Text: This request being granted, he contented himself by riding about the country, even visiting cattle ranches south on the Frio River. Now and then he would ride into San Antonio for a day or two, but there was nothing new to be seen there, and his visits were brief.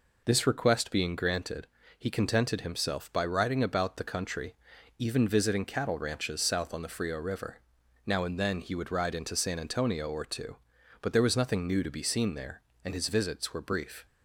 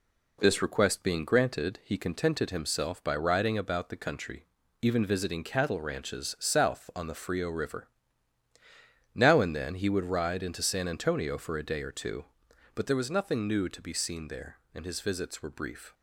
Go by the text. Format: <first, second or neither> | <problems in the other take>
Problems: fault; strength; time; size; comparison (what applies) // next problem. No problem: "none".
second | skips "for a day"; at 10.0 s